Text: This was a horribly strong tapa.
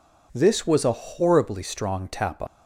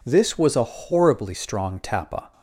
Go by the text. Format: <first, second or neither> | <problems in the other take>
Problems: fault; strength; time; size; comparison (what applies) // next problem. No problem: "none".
second | leaves "tapa" unfinished; at 2.4 s; 135 ms